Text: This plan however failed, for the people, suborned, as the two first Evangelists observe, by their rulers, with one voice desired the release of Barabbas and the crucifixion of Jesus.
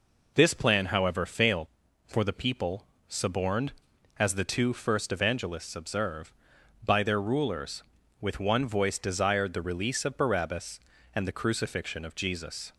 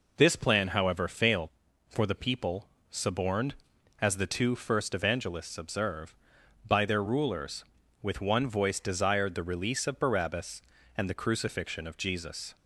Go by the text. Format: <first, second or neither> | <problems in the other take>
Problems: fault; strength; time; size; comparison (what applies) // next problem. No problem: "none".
neither | none